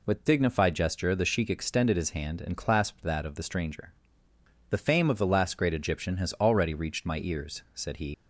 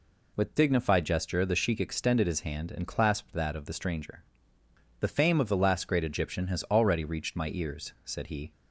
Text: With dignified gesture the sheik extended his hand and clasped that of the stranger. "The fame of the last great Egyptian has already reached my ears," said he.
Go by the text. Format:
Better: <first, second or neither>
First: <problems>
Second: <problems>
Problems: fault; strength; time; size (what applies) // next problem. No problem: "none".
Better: second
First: leaves "he" unfinished; at 8.1 s; 70 ms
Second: none